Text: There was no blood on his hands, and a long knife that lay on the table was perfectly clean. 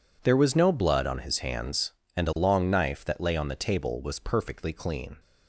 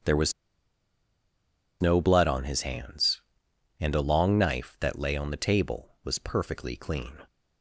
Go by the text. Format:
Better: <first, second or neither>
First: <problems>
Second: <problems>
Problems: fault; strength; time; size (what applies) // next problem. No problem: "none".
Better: first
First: none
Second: starts louder than the rest; strong; until 2.5 s; 8 dB // pauses between "was" and "no"; strong; at 0.3 s; 1.4 s long